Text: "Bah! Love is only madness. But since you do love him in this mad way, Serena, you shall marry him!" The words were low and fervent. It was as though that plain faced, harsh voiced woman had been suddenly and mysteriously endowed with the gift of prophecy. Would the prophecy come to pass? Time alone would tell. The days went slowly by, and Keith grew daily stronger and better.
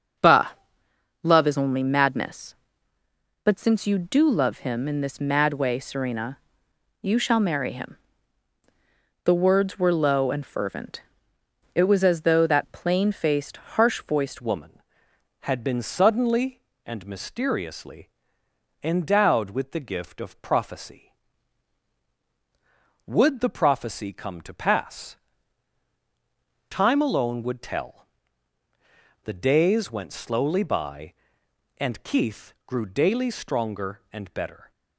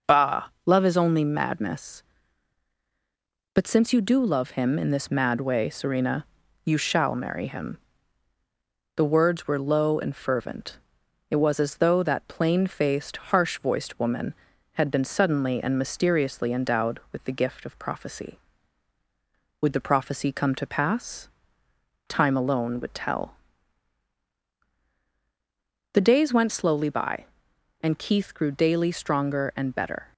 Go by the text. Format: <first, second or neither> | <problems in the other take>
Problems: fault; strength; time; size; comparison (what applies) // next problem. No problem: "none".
second | starts louder than the rest; until 1.8 s; 6.5 dB; noticeable in the second // changes voice at "woman"; from 14.4 s on; 20.3 s long // pauses between "mysteriously" and "endowed"; noticeable; at 18.0 s; 0.74 s long